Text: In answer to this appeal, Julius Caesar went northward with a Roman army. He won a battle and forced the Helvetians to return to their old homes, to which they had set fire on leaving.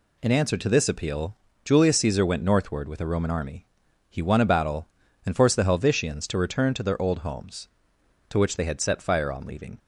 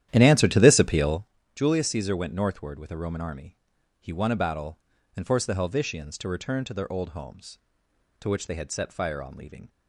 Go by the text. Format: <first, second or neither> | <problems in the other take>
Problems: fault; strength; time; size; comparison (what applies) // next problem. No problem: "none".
first | starts louder than the rest; strong; until 1.3 s; 11.5 dB